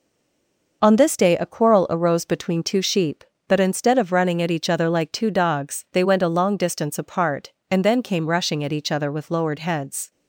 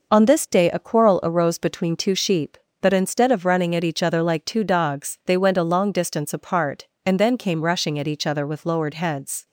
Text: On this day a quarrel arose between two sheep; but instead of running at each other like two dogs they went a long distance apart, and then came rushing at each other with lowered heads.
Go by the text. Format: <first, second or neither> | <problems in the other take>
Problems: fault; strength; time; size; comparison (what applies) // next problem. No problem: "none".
second | stays silent before the first word; slight; until 0.8 s; 0.8 s long